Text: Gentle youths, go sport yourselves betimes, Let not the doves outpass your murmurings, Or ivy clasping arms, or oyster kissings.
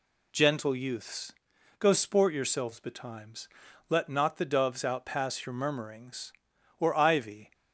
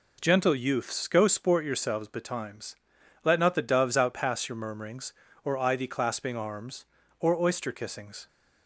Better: second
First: stops before "clasping arms or oyster kissings"; at 7.5 s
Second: none

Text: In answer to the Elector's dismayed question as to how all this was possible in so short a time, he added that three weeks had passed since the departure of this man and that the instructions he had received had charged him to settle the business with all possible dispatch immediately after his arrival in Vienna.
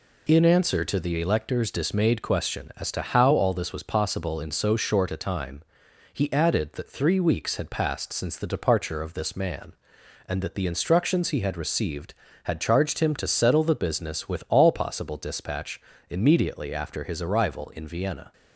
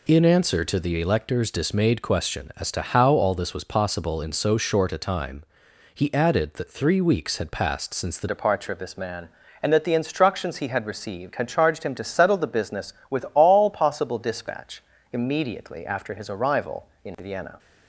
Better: first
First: pauses between "dispatch" and "immediately"; slight; at 15.8 s; 0.30 s long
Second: changes voice at "departure"; from 8.2 s on; 9.3 s long // pauses between "dispatch" and "immediately"; slight; at 14.8 s; 0.30 s long

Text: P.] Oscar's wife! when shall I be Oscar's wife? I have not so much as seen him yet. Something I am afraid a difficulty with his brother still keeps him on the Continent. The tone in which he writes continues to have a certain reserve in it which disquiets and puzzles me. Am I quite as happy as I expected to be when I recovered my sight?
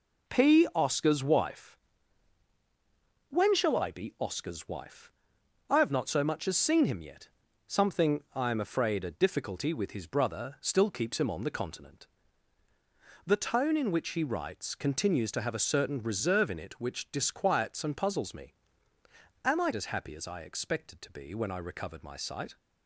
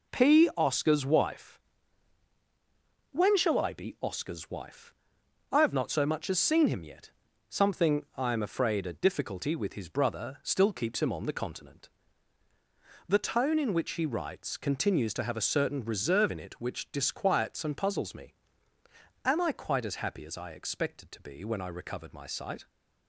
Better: second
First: skips "quite"; at 19.7 s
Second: none

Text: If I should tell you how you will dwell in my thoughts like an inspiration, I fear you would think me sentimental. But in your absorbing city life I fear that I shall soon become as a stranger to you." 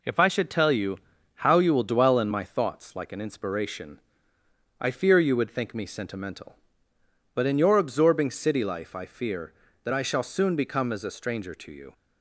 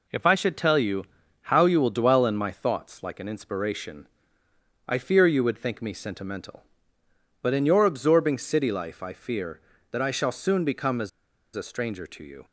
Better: first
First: pauses between "you" and "how"; at 0.9 s; 0.40 s long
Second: pauses between "you" and "how"; at 1.0 s; 0.40 s long // pauses between "as" and "a"; at 11.0 s; 0.44 s long

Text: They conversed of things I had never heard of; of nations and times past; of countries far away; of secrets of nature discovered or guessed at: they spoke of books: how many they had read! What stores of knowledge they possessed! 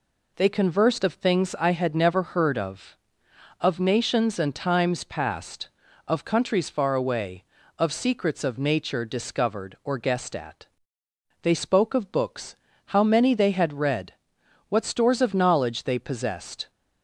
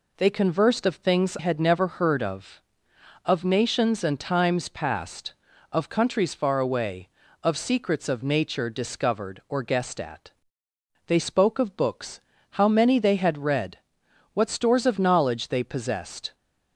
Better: first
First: none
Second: skips "I"; at 1.3 s

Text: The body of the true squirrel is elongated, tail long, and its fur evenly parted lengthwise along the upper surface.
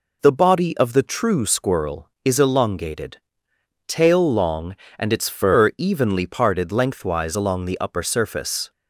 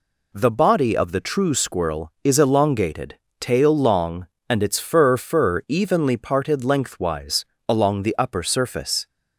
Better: first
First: none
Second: says "fur" twice; at 5.1 s // pauses between "lengthwise" and "along"; slight; at 7.4 s; 0.22 s long

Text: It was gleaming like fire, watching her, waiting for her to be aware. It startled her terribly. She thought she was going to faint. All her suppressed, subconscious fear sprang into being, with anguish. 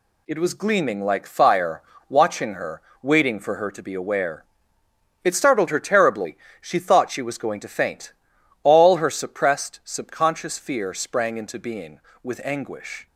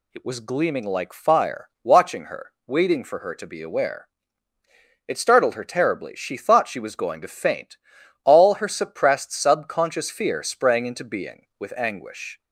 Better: neither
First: none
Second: none

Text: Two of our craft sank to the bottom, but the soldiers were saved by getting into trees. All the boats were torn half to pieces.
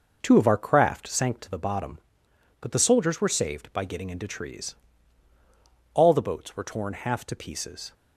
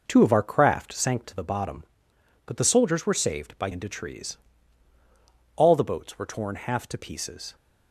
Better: first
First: none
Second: skips "getting"; at 3.7 s

